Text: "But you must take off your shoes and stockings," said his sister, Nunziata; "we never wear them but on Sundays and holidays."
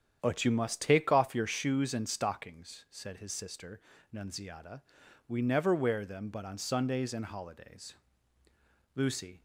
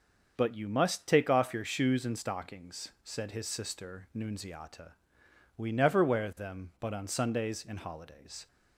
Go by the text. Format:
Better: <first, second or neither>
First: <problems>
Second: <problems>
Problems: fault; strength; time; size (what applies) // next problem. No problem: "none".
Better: second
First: starts louder than the rest; strong; until 1.2 s; 9 dB // goes on to say "Lucy"; slight; from 8.9 s on; 0.46 s long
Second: starts louder than the rest; until 1.3 s; 6.5 dB